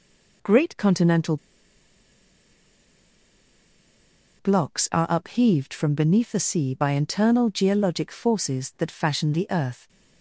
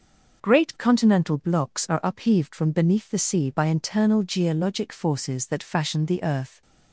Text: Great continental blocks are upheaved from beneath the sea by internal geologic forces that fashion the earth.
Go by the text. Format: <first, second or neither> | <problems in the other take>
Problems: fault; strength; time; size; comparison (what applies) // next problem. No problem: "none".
second | pauses between "continental" and "blocks"; strong; at 1.3 s; 3.0 s long